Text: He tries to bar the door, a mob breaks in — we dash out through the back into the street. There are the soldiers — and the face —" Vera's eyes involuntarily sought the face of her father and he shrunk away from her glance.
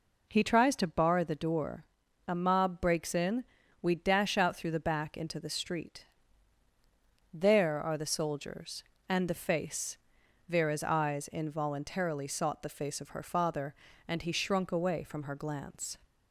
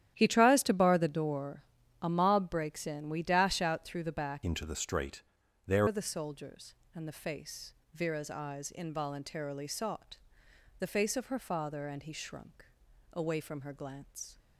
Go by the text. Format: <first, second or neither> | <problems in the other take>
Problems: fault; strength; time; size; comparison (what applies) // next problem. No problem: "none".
first | starts louder than the rest; strong; until 1.1 s; 11 dB // changes voice from "into" to "There"; from 4.4 to 5.8 s; 1.4 s long // pauses between "sought" and "the"; noticeable; at 10.1 s; 0.62 s long // pauses between "shrunk" and "away"; noticeable; at 12.6 s; 0.48 s long